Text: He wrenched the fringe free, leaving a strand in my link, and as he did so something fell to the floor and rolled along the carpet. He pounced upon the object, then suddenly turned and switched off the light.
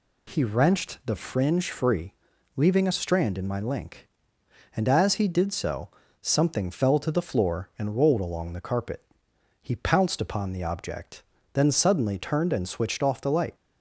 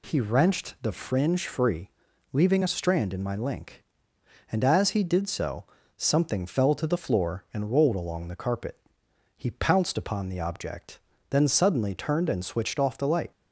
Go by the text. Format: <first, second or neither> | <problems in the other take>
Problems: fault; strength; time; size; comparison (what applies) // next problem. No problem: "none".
neither | pauses between "so" and "something"; slight; the same in both